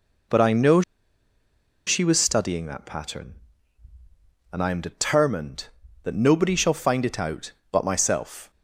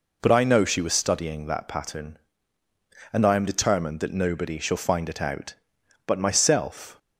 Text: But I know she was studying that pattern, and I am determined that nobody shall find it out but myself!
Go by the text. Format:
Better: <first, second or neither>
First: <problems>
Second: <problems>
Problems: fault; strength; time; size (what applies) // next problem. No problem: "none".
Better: second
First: pauses between "know" and "she"; at 0.8 s; 1.0 s long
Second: none